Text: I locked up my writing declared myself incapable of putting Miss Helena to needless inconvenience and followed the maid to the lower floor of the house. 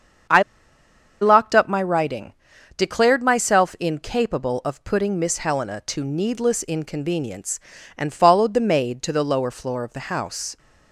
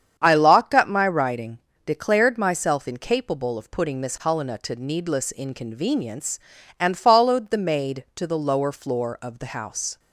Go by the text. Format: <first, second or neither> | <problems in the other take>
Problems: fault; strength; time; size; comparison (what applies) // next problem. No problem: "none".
second | starts louder than the rest; strong; until 2.1 s; 7.5 dB; strong in the second // pauses between "I" and "locked"; noticeable; at 0.4 s; 0.79 s long // pauses between "writing" and "declared"; noticeable; at 2.3 s; 0.46 s long; slight in the second